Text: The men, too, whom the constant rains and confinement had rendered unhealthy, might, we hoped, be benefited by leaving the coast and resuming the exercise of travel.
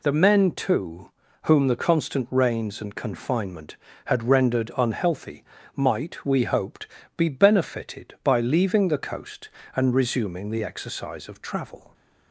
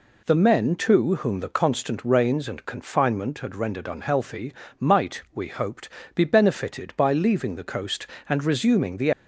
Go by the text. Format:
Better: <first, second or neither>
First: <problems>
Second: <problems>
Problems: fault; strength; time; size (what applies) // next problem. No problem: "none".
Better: first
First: none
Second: stops before "exercise of travel"; at 9.1 s